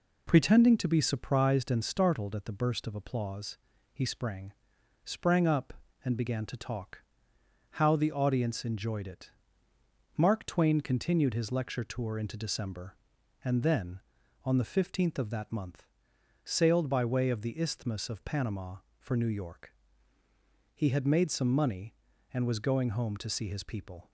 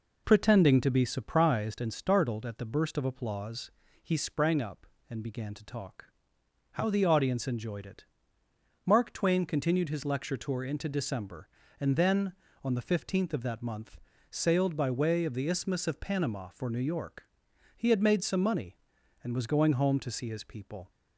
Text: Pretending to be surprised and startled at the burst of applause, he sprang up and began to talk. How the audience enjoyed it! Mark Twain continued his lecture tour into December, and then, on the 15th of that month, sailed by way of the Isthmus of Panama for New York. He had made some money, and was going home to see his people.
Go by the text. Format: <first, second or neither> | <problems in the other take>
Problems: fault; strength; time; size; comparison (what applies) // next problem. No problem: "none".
second | says "sprang" twice; at 5.0 s